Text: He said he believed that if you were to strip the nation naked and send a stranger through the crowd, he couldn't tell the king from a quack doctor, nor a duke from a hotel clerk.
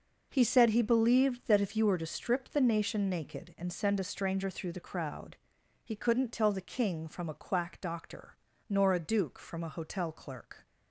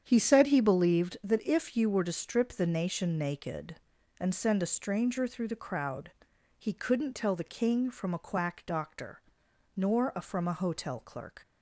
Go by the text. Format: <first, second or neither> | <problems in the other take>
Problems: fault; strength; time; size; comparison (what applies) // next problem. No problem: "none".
first | starts louder than the rest; strong; until 1.0 s; 8.5 dB // skips "duke"; at 10.1 s